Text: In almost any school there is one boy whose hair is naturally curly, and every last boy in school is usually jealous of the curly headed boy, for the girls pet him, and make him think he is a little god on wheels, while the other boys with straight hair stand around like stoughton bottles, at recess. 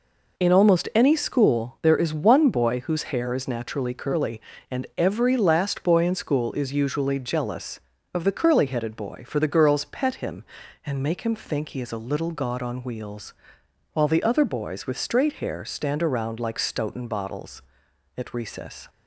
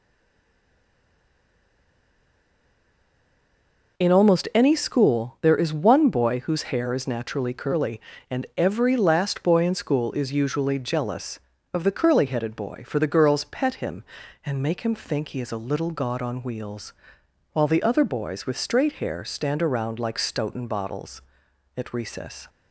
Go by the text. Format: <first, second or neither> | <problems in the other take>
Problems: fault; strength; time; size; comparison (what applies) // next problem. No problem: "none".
first | stays silent before the first word; strong; until 3.9 s; 3.9 s long